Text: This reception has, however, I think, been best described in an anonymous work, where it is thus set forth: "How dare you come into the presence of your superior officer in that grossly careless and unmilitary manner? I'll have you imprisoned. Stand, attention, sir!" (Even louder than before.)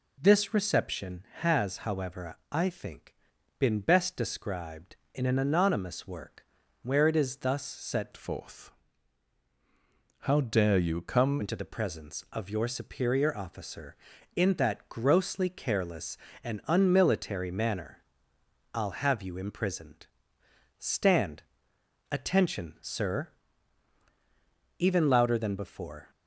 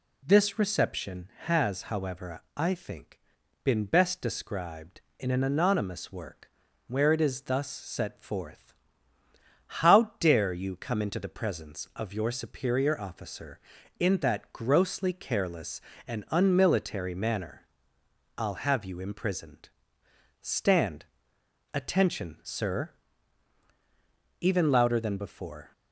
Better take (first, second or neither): second